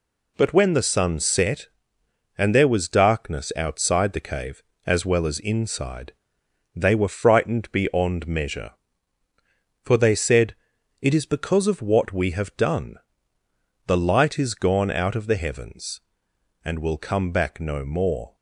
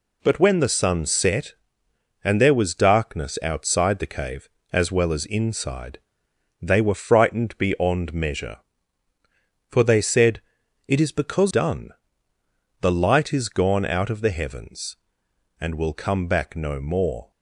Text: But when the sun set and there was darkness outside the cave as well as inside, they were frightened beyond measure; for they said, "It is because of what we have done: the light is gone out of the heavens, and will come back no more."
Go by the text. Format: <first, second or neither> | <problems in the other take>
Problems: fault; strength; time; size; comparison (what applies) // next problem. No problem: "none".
first | skips "of what we have"; at 11.5 s